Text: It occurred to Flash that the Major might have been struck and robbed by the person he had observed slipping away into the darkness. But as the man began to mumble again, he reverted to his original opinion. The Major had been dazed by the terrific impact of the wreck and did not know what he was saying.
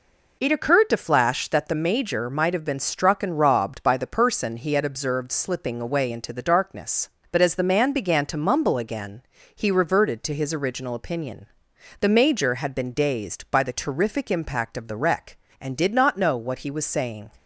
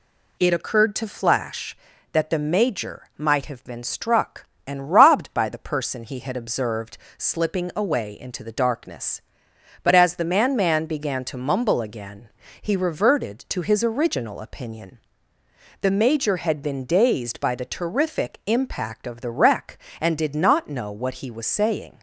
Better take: first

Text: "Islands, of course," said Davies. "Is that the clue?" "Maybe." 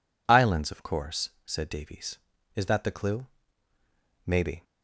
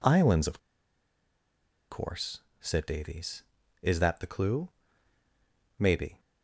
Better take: first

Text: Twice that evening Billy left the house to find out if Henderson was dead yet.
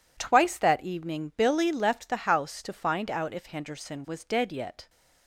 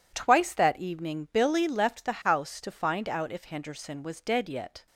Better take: neither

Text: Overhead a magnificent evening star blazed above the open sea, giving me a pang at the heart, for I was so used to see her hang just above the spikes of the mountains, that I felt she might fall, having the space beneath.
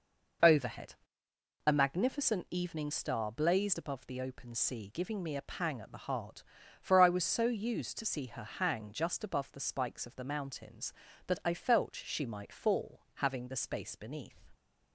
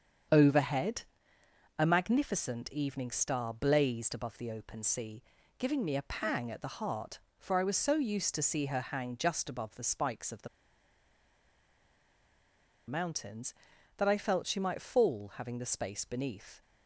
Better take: first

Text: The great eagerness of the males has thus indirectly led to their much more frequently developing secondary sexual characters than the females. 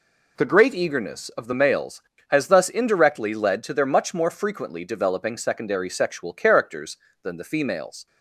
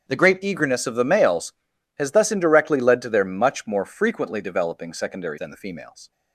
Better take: first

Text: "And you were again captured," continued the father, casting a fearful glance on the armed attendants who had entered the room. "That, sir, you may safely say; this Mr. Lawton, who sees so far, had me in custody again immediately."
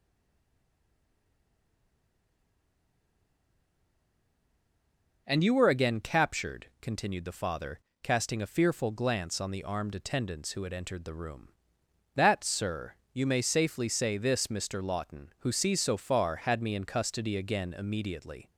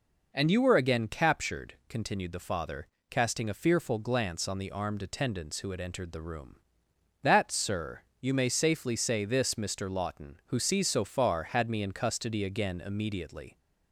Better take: second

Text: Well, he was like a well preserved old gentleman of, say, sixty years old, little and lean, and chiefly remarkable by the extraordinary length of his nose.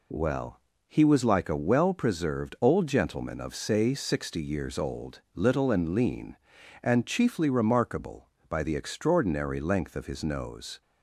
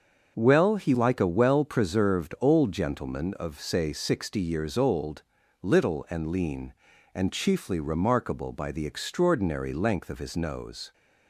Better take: first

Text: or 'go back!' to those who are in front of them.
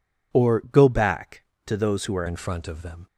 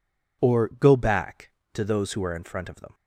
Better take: second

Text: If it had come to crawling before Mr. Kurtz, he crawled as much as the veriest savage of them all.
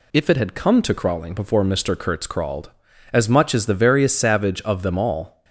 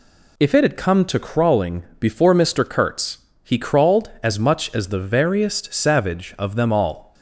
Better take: second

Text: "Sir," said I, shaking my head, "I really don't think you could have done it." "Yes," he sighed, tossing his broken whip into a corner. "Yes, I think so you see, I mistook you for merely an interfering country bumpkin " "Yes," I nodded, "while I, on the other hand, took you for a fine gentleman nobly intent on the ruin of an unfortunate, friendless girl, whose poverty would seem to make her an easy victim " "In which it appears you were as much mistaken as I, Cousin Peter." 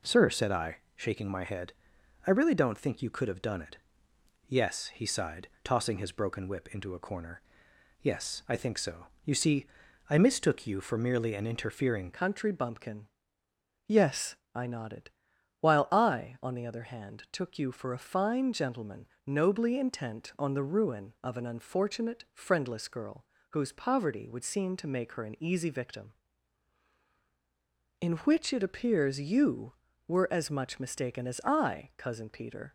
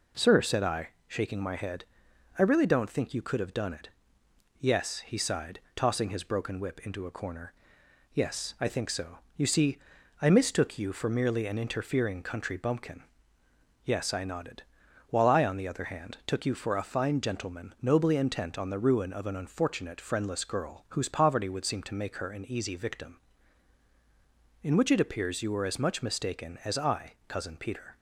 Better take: second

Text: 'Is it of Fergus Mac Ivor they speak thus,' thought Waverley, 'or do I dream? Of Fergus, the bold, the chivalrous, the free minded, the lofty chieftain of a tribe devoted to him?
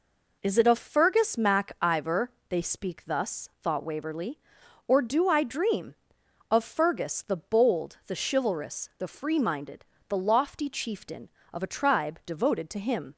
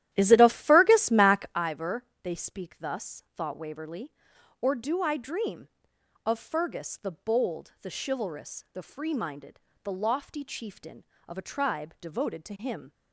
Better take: first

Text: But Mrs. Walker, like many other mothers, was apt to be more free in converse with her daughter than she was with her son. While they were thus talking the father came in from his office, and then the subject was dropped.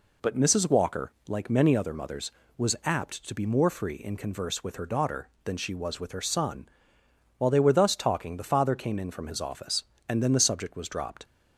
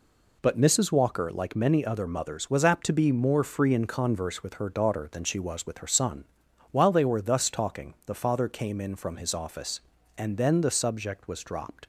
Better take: neither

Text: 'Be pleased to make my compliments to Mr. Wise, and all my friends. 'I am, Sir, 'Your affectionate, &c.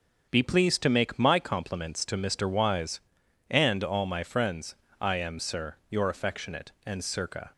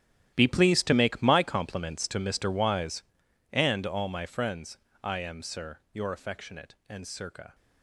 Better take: first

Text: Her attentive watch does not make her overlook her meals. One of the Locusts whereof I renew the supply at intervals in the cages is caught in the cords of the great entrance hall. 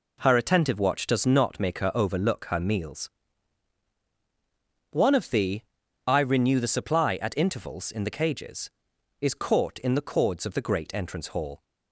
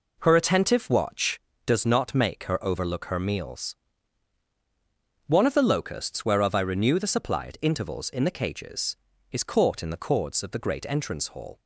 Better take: second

